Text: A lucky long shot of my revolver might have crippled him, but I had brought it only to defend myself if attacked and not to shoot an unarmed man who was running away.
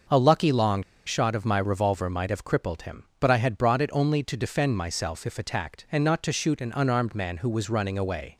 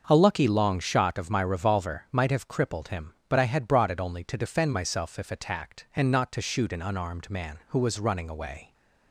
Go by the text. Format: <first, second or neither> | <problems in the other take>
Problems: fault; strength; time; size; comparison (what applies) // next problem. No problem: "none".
second | starts louder than the rest; until 1.3 s; 6 dB; also in the second // pauses between "long" and "shot"; slight; at 0.8 s; 0.24 s long